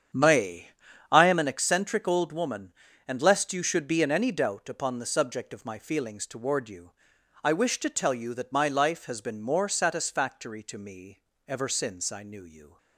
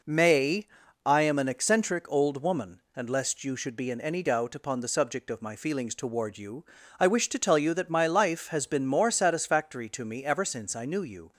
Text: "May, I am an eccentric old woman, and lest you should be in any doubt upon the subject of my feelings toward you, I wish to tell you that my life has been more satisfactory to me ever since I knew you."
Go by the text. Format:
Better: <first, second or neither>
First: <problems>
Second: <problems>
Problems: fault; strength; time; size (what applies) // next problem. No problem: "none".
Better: second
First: starts louder than the rest; strong; until 1.6 s; 8.5 dB // pauses between "me" and "ever"; slight; at 11.2 s; 0.26 s long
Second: none